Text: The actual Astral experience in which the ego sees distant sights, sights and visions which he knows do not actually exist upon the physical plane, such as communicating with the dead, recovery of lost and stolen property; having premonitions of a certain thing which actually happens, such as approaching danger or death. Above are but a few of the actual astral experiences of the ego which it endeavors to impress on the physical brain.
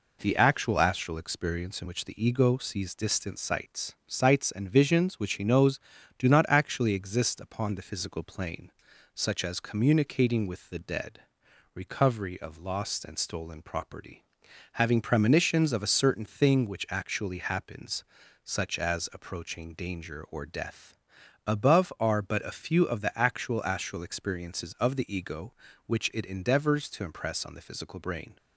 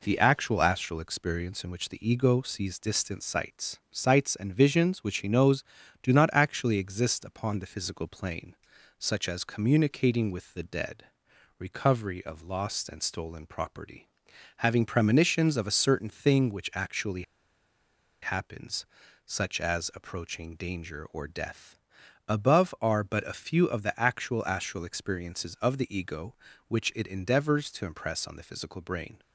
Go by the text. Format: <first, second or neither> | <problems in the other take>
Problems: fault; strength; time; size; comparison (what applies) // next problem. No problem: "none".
first | pauses between "actually" and "happens"; at 17.2 s; 1.0 s long